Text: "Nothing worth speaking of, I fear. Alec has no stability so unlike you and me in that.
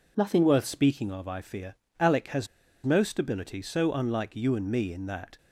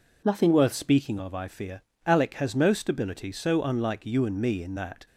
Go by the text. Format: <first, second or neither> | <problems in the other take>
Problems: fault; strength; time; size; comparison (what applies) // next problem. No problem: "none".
second | pauses between "has" and "no"; at 2.4 s; 0.37 s long